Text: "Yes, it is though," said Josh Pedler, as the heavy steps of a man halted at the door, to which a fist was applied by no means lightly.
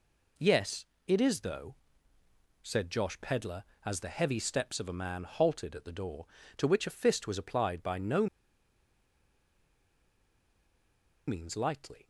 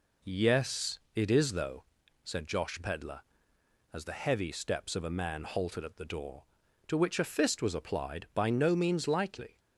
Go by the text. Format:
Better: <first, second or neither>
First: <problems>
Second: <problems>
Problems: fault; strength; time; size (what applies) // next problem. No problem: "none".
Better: second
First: pauses between "no" and "means"; strong; at 8.2 s; 3.0 s long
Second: none